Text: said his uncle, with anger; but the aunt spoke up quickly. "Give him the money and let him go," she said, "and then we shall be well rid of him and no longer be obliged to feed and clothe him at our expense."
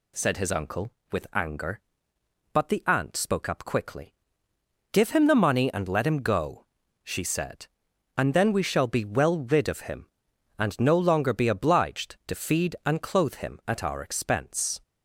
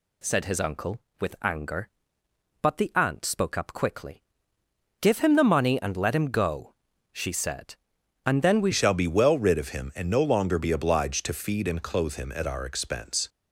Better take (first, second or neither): first